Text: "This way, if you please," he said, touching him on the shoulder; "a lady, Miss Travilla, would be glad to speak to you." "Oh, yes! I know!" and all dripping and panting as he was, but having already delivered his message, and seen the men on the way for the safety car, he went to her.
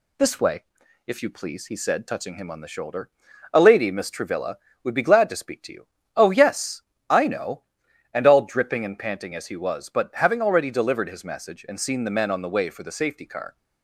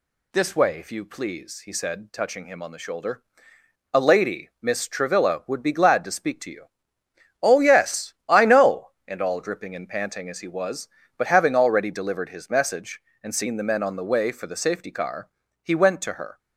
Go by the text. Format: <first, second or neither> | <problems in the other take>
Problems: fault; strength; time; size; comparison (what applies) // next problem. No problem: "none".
second | stops before "he went to her"; at 13.5 s